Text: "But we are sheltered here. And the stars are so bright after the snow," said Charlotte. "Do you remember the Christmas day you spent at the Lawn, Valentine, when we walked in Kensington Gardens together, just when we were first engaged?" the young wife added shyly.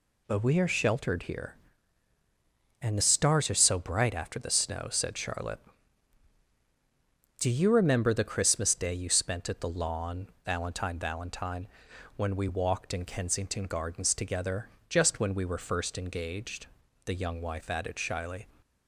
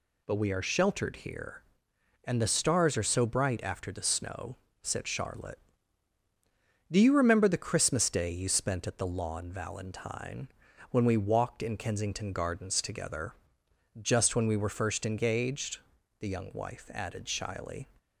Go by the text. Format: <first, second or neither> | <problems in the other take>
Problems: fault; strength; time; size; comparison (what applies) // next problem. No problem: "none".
second | says "Valentine" twice; at 10.9 s